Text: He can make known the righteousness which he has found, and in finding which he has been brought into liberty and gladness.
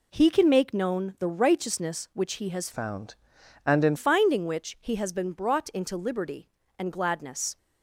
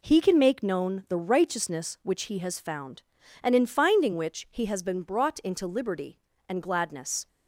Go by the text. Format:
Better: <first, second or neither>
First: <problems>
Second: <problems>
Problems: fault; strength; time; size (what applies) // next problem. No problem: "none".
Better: second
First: changes voice from "found" to "in"; from 2.7 to 3.9 s; 1.2 s long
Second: none